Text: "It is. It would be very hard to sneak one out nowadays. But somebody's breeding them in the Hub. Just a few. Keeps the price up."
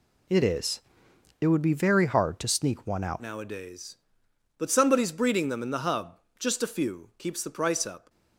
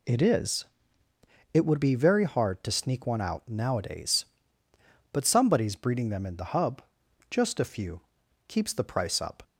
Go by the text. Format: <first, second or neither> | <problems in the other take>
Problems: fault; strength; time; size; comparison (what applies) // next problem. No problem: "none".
second | changes voice at "nowadays"; from 3.2 s on; 4.8 s long